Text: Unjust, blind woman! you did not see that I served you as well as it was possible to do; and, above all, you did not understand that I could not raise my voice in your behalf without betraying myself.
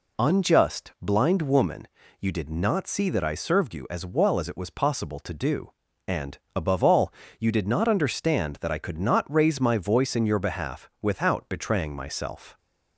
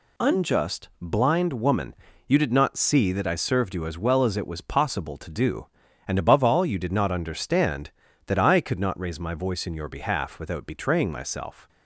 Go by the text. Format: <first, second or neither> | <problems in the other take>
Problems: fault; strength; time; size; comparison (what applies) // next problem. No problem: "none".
neither | none